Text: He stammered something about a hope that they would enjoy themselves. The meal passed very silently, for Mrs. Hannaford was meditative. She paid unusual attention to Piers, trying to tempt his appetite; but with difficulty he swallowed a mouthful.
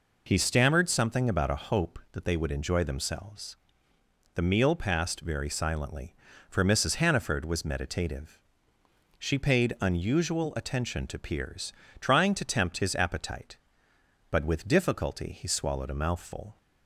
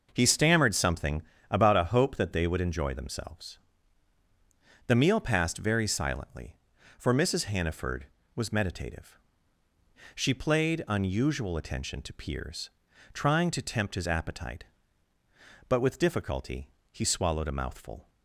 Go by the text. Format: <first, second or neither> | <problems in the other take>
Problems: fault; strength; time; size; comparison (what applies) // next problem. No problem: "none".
first | pauses between "something" and "about"; slight; at 1.2 s; 0.28 s long // says "played" for "paid"; at 10.3 s // pauses between "difficulty" and "he"; slight; at 16.6 s; 0.22 s long